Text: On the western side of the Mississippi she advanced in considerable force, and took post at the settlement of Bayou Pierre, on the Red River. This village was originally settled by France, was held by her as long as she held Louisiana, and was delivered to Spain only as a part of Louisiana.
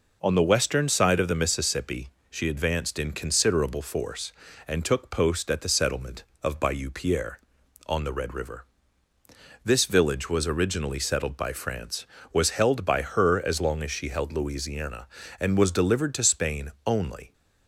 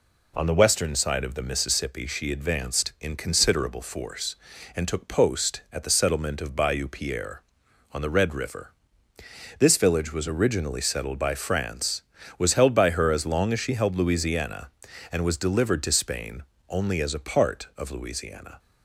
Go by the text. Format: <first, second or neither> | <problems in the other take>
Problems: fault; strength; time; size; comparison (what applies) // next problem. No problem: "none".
second | pauses between "Mississippi" and "she"; slight; at 2.0 s; 0.20 s long // pauses between "Spain" and "only"; slight; at 16.7 s; 0.16 s long; slight in the second // stops before "as a part of Louisiana"; at 17.3 s